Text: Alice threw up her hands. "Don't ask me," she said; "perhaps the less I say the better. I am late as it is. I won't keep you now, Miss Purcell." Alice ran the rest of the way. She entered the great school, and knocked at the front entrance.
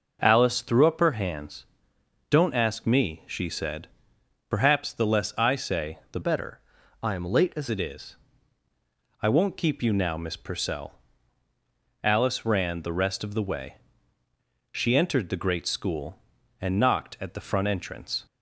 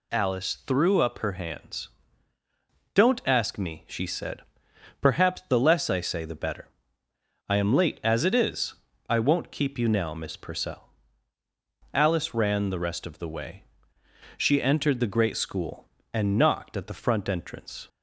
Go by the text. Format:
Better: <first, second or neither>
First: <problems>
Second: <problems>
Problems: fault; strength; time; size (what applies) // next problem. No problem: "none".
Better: second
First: changes voice from "better" to "as"; from 6.2 to 7.6 s; 1.4 s long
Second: none